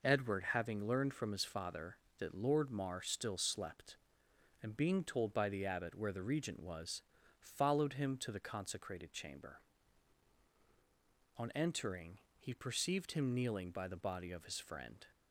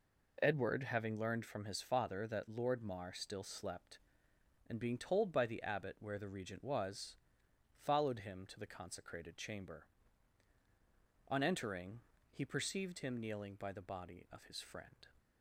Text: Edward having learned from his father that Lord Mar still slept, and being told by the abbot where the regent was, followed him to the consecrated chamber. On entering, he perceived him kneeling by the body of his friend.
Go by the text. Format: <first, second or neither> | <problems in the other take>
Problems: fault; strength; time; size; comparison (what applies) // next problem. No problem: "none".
neither | none